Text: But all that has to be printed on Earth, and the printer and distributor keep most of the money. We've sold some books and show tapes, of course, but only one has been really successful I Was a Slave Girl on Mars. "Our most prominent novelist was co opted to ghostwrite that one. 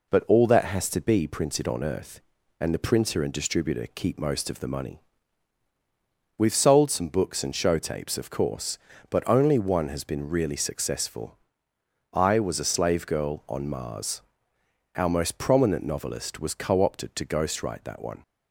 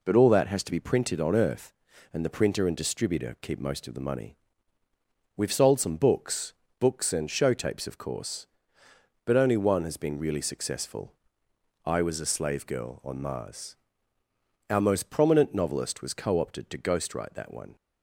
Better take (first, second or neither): first